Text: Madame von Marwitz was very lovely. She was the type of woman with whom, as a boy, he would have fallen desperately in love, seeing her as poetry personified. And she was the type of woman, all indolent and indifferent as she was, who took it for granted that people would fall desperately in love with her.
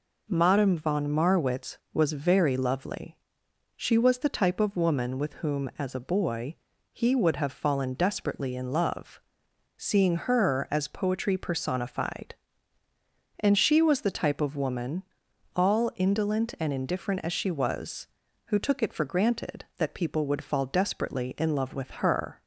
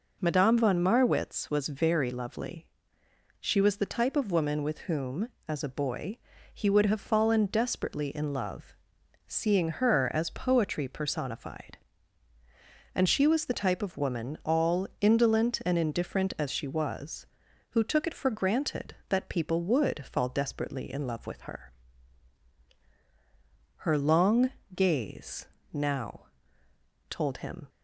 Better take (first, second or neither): first